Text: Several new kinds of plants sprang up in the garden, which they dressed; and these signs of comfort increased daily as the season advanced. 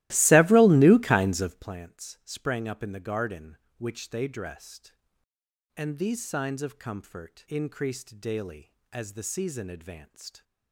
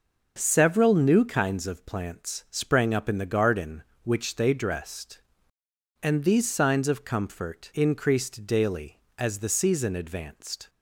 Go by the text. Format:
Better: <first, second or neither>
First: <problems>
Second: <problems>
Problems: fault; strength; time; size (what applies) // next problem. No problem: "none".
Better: second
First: starts louder than the rest; strong; until 1.8 s; 16.5 dB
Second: none